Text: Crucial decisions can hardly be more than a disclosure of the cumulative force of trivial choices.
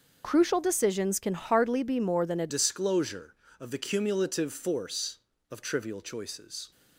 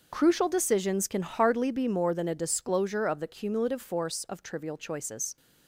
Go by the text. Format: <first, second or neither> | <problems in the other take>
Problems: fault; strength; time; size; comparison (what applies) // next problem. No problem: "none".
second | starts louder than the rest; noticeable; until 1.2 s; 6 dB; also in the second // changes voice at "disclosure"; from 2.4 s on; 4.3 s long